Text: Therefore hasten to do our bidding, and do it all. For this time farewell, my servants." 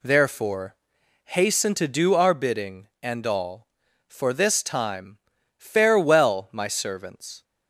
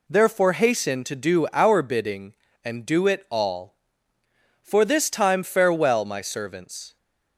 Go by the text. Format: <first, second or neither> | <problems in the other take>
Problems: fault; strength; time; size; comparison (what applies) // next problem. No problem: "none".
second | pauses between "Therefore" and "hasten"; noticeable; at 0.7 s; 0.50 s long // skips "do it"; at 3.2 s // pauses between "time" and "farewell"; at 5.1 s; 0.38 s long